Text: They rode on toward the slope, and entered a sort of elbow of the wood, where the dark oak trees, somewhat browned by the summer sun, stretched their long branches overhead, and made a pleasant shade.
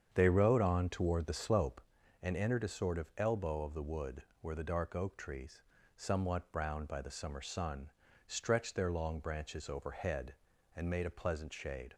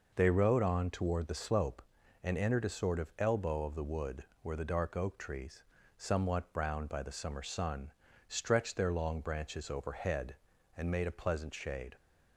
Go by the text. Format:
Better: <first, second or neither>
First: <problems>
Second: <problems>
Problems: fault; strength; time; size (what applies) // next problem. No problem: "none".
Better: second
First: starts louder than the rest; strong; until 1.9 s; 7.5 dB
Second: none